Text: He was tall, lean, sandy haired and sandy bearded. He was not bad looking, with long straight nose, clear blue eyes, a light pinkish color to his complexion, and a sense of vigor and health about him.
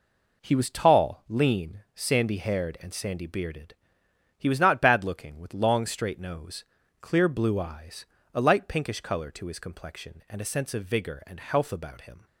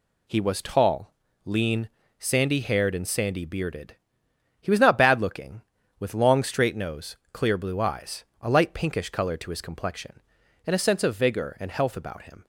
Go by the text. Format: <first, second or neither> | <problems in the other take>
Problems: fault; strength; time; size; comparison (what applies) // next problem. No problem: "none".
neither | none